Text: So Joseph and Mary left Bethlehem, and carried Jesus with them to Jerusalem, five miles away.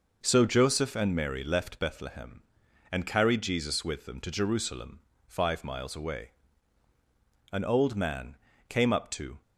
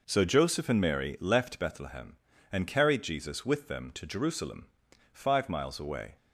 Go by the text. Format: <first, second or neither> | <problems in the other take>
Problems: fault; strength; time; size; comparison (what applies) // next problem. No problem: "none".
second | goes on to say "An old man came up to"; strong; from 7.5 s on; 1.9 s long